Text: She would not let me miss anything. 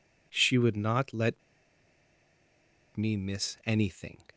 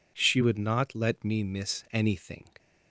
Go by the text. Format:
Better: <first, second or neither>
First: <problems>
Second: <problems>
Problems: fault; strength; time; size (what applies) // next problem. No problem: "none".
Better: second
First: pauses between "let" and "me"; strong; at 1.4 s; 1.5 s long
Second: none